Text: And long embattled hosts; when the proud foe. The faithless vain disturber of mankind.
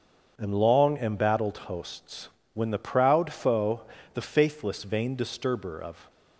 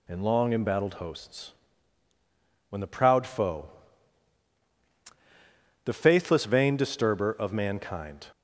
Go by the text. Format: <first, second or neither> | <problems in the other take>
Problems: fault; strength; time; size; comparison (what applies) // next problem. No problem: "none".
second | starts louder than the rest; until 1.3 s; 7 dB // stops before "mankind"; at 6.0 s